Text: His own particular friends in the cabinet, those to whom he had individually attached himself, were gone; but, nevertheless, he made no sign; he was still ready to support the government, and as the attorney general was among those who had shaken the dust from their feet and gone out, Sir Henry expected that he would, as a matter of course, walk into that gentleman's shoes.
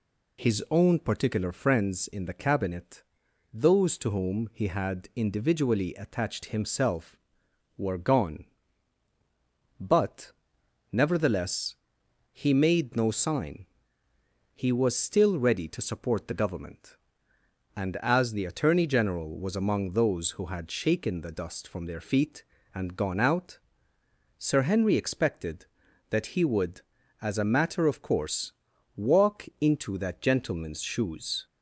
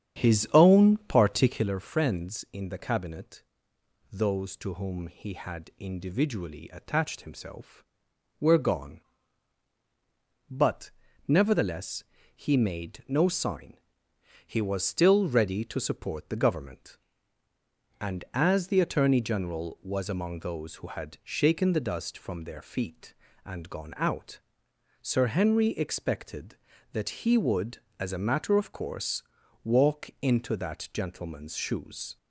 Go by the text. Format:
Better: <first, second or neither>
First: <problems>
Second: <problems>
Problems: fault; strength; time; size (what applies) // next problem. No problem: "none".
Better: first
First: none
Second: starts louder than the rest; strong; until 1.7 s; 8.5 dB